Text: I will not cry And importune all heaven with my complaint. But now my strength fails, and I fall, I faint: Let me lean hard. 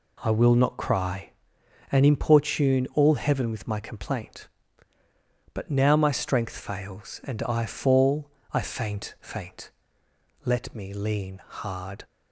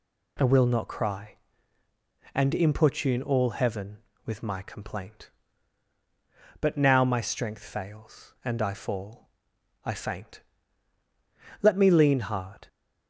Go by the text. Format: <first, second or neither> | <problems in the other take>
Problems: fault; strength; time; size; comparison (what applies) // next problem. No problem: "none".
second | says "faint" twice; at 9.2 s